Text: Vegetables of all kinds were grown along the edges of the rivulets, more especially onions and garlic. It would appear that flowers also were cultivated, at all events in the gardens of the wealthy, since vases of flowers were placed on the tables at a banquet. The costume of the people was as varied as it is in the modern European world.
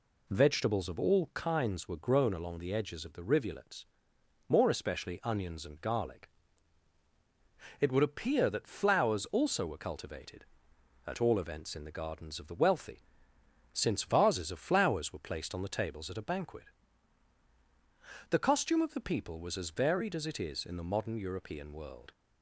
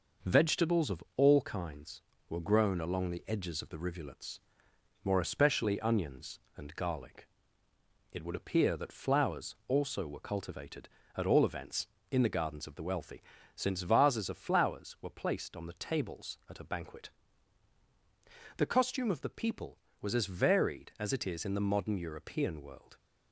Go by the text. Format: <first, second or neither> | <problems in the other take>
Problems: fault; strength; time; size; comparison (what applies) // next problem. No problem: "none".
first | gets quieter; noticeable; throughout; 4.5 dB // pauses between "of" and "all"; slight; at 1.0 s; 0.16 s long